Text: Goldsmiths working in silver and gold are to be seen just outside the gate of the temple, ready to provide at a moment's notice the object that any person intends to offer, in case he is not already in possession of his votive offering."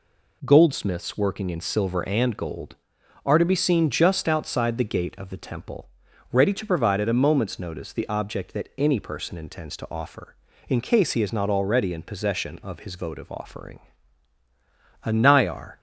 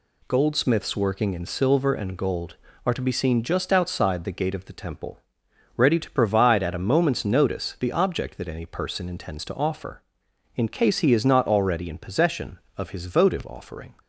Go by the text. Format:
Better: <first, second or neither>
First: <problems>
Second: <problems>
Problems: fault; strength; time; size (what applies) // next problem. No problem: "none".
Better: second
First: goes on to say "A Nayar"; noticeable; from 15.0 s on; 0.76 s long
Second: none